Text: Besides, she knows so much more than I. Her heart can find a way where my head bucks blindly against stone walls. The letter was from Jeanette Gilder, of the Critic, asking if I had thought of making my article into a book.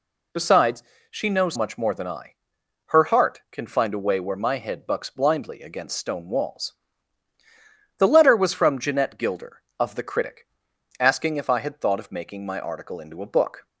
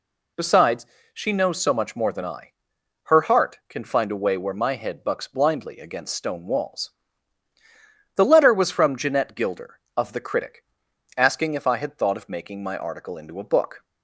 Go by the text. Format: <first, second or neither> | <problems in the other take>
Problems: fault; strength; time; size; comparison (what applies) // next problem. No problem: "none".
second | skips "so"; at 1.5 s